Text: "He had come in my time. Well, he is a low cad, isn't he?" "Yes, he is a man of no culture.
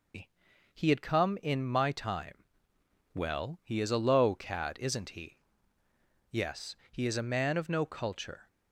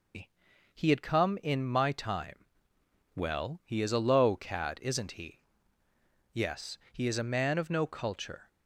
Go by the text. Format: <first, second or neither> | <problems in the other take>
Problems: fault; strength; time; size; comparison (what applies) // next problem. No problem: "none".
neither | none